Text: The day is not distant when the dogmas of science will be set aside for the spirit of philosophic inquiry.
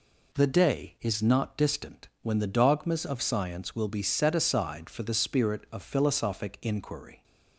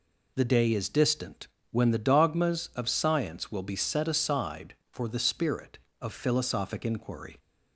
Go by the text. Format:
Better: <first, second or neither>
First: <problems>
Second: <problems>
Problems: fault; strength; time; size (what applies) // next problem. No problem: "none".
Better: first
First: none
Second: skips "not"; at 0.8 s // pauses between "distant" and "when"; slight; at 1.4 s; 0.23 s long